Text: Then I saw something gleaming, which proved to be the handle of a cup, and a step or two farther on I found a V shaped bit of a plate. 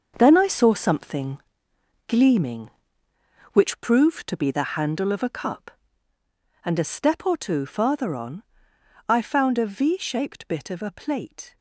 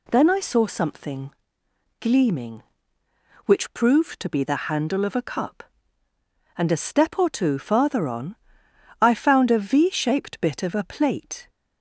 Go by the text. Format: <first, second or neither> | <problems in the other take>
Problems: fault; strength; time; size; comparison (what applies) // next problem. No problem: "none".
second | gets quieter; strong; throughout; 10.5 dB // pauses between "something" and "gleaming"; noticeable; at 1.3 s; 0.68 s long; noticeable in the second // pauses between "on" and "I"; noticeable; at 8.4 s; 0.66 s long; noticeable in the second